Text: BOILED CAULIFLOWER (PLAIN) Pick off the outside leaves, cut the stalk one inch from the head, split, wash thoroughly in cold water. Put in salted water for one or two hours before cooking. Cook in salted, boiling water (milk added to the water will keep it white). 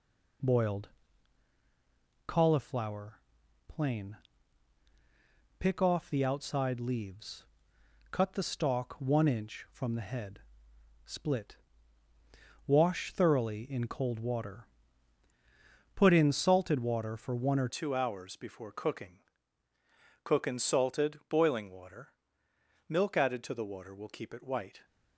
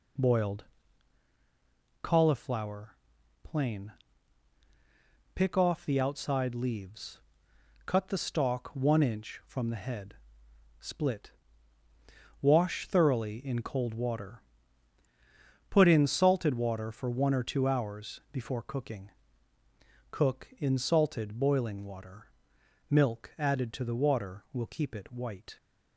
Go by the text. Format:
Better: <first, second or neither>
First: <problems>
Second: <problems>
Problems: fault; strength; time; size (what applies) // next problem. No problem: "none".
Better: second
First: pauses between "BOILED" and "CAULIFLOWER"; strong; at 0.8 s; 1.4 s long // changes voice at "two"; from 17.6 s on; 7.2 s long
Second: pauses between "BOILED" and "CAULIFLOWER"; strong; at 0.6 s; 1.4 s long